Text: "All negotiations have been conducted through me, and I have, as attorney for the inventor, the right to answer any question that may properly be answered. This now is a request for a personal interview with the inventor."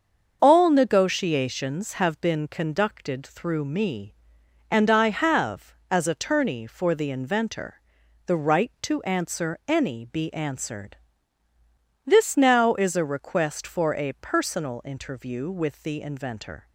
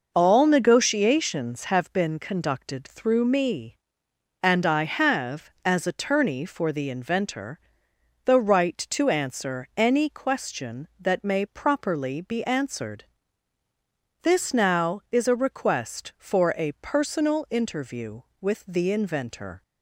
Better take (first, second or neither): second